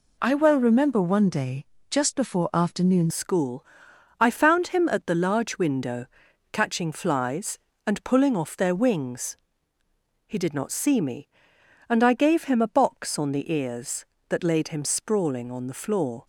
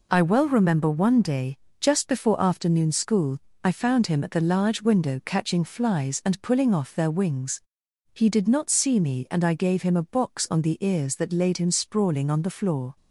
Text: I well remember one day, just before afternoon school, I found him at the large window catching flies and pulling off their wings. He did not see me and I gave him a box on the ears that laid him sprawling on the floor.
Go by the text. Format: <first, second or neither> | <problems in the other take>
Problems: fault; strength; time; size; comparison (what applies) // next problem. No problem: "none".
second | changes voice at "school"; from 3.1 s on; 13.1 s long // pauses between "window" and "catching"; at 6.0 s; 0.44 s long